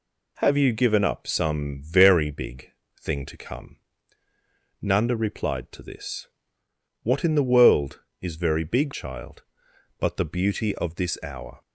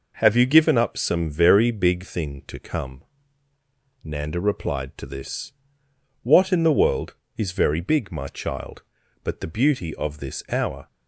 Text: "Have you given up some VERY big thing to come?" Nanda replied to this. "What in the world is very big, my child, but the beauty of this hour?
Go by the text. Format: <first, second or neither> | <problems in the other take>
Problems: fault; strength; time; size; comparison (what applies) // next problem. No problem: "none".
second | pauses between "big" and "thing"; slight; at 2.7 s; 0.30 s long // skips "my"; at 8.9 s